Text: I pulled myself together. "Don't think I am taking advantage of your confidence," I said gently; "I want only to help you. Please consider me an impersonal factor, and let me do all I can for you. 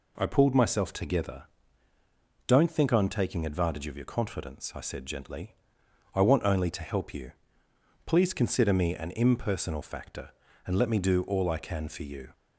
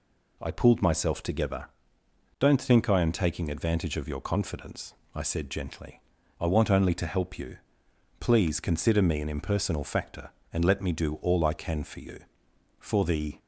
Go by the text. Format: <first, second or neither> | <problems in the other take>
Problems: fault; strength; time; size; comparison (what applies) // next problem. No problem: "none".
first | goes on to say "For the"; from 12.7 s on; 0.60 s long